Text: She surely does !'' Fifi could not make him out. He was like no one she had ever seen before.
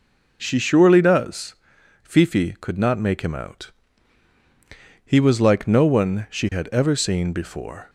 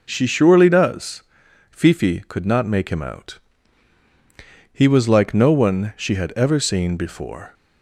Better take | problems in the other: neither | none

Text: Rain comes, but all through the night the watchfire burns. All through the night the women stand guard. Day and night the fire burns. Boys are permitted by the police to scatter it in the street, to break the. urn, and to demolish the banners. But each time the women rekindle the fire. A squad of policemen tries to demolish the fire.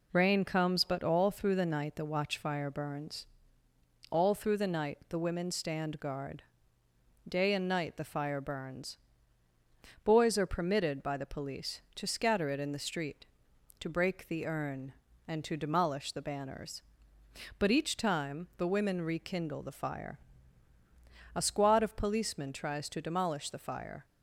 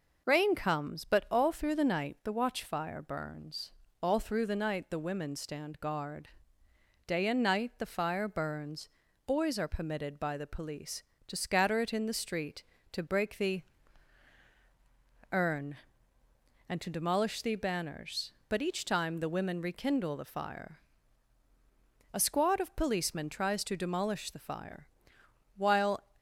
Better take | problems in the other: first | goes on to say "While"; slight; from 25.5 s on; 0.46 s long

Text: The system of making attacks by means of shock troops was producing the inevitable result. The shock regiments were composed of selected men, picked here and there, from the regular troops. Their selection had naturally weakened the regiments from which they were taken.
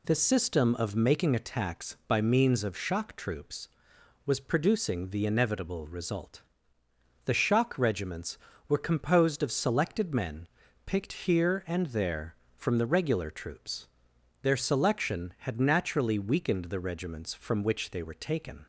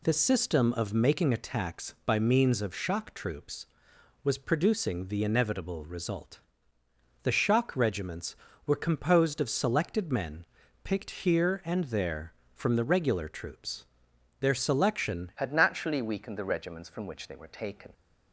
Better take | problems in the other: first | changes voice at "had"; from 15.3 s on; 2.6 s long

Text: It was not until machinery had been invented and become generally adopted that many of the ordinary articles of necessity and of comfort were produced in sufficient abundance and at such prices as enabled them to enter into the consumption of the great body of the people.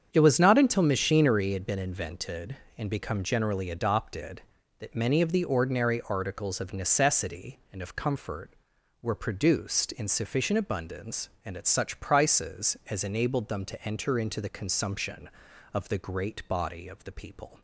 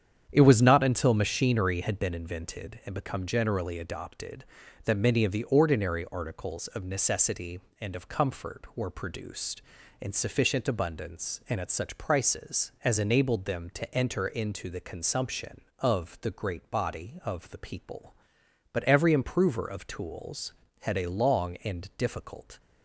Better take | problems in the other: first | starts louder than the rest; strong; until 1.3 s; 8.5 dB; strong in the first // goes on to say "But every improver of tools had a long and difficult"; strong; from 18.7 s on; 3.8 s long

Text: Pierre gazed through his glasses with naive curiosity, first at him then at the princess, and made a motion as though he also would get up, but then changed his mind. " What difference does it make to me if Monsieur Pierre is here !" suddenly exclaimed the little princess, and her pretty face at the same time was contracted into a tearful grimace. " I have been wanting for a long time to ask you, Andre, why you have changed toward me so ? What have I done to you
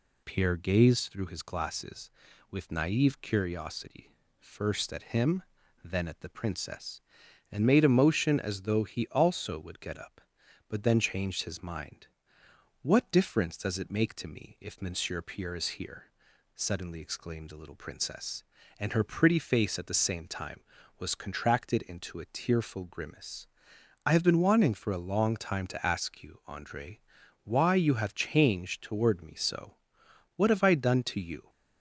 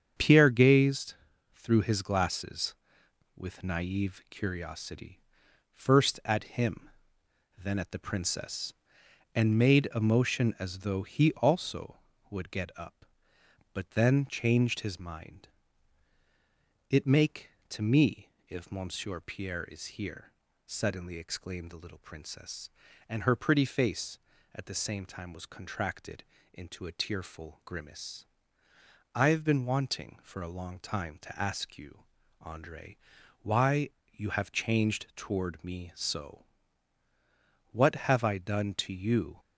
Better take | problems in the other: first | starts louder than the rest; strong; until 1.5 s; 8 dB // pauses between "gazed" and "through"; at 1.1 s; 0.40 s long // pauses between "him" and "then"; noticeable; at 6.8 s; 0.70 s long; also in the first // skips "What difference does"; at 16.8 s // pauses between "me" and "if"; slight; at 18.2 s; 0.18 s long // pauses between "contracted" and "into"; slight; at 26.2 s; 0.30 s long // pauses between "why" and "you"; slight; at 33.8 s; 0.24 s long

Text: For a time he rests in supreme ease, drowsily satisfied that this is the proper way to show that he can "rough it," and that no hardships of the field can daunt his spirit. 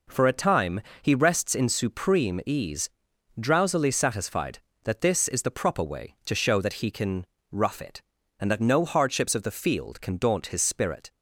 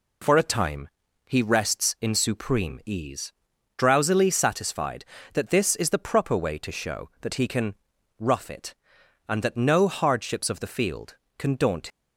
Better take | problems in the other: first | pauses between "time" and "he"; at 0.8 s; 0.40 s long; slight in the first // pauses between "can" and "rough"; noticeable; at 7.7 s; 0.46 s long; slight in the first // stops before "his spirit"; at 11.8 s

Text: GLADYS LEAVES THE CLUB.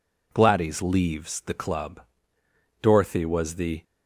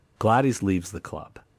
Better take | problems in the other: second | goes on to say "Dorothy was the"; noticeable; from 2.8 s on; 1.0 s long

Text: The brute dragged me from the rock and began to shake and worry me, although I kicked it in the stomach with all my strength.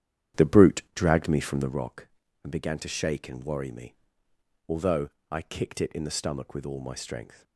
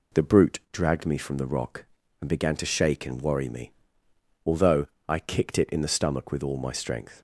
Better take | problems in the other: second | starts louder than the rest; strong; until 1.9 s; 10 dB // pauses between "although" and "I"; slight; at 5.0 s; 0.22 s long; slight in the second

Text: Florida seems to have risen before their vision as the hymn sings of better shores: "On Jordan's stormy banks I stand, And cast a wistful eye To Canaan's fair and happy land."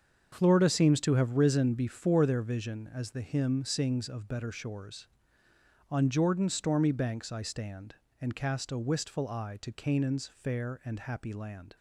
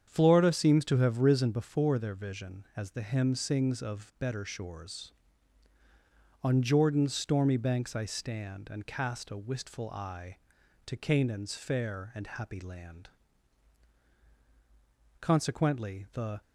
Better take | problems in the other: first | starts louder than the rest; strong; until 1.0 s; 8 dB; also in the first // goes on to say "Consequently the"; noticeable; from 15.2 s on; 1.2 s long

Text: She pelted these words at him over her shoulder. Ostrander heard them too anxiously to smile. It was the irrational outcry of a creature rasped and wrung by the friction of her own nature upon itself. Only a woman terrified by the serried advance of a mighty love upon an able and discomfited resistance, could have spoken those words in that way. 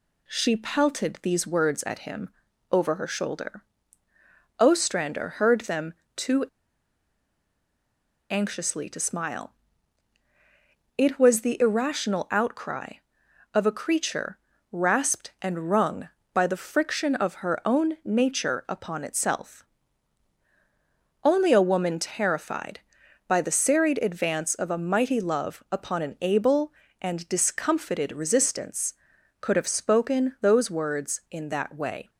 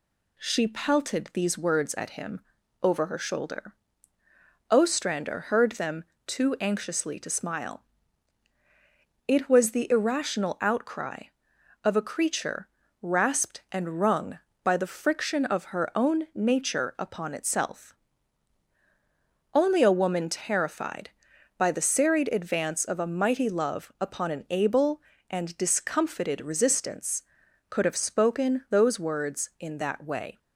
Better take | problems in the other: second | pauses between "him" and "over"; at 2.2 s; 0.42 s long; also in the second // pauses between "them" and "too"; slight; at 5.9 s; 0.24 s long; slight in the second // pauses between "too" and "anxiously"; strong; at 6.4 s; 1.8 s long // pauses between "creature" and "rasped"; slight; at 14.3 s; 0.34 s long; slight in the second

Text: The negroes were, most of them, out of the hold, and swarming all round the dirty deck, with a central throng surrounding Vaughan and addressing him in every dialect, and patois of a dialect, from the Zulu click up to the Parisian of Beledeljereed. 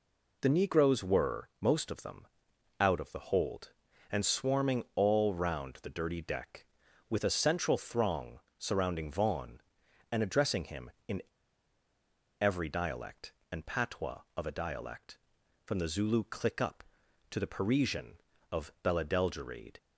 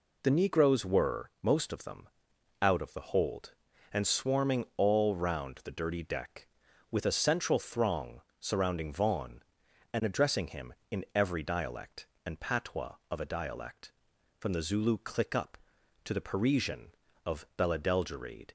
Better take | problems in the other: second | pauses between "throng" and "surrounding"; slight; at 8.3 s; 0.20 s long; slight in the second // pauses between "in" and "every"; at 11.2 s; 1.1 s long

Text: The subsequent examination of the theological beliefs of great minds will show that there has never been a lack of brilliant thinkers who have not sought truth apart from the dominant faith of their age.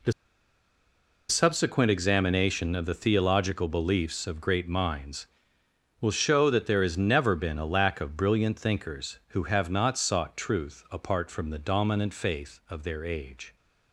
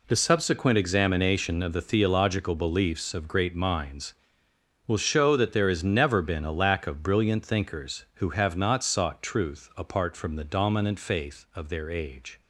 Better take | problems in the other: second | pauses between "The" and "subsequent"; at 0.1 s; 1.1 s long

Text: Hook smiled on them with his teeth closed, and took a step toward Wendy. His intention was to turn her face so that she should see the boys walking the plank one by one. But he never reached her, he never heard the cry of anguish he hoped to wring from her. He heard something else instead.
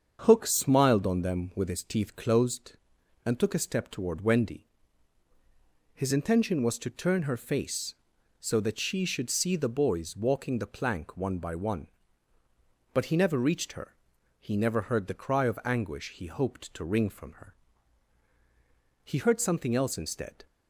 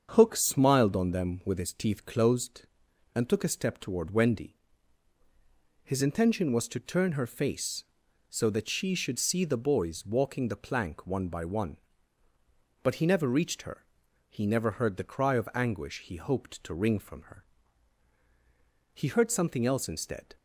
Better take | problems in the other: neither | starts louder than the rest; strong; the same in both

